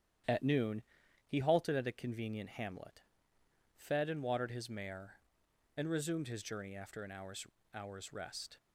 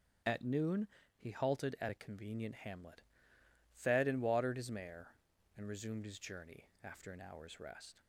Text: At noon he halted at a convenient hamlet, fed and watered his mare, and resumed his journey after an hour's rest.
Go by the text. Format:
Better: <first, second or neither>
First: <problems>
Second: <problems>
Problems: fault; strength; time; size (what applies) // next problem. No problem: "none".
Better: second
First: starts louder than the rest; strong; until 1.7 s; 10 dB // pauses between "noon" and "he"; at 0.8 s; 0.44 s long // says "hour's" twice; at 7.7 s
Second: starts louder than the rest; until 1.5 s; 6.5 dB // pauses between "noon" and "he"; slight; at 0.8 s; 0.30 s long